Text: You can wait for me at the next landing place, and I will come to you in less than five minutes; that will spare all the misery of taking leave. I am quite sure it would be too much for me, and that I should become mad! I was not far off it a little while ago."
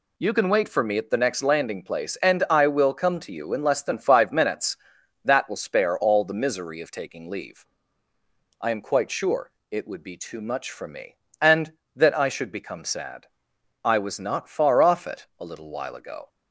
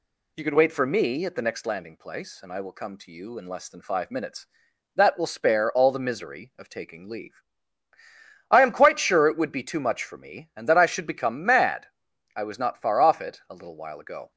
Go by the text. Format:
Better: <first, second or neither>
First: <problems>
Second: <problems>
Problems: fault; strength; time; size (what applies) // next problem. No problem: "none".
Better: second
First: pauses between "sure" and "it"; slight; at 9.5 s; 0.22 s long // says "sad" for "mad"; at 12.8 s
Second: none